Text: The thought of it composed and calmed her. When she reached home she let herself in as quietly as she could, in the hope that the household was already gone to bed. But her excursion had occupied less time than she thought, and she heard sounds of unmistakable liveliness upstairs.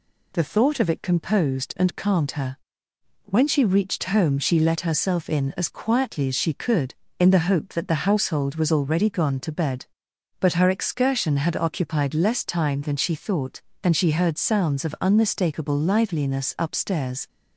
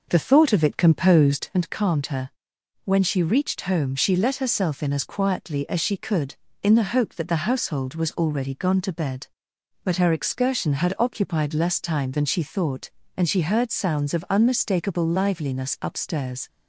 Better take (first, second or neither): first